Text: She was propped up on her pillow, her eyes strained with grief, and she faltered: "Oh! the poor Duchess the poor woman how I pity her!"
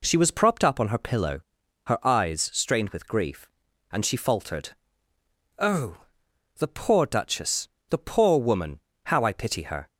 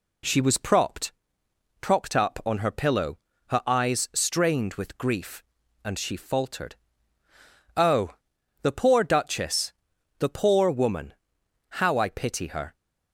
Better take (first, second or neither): first